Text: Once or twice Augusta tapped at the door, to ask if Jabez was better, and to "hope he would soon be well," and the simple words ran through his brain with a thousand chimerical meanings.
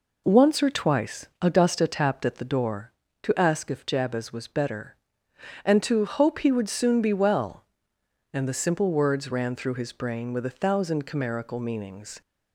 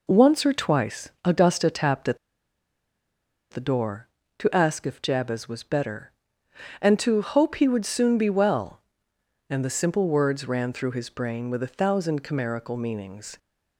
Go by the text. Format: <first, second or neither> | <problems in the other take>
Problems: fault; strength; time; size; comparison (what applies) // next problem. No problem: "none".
first | pauses between "twice" and "Augusta"; slight; at 1.0 s; 0.16 s long; slight in the first // pauses between "at" and "the"; strong; at 2.1 s; 1.3 s long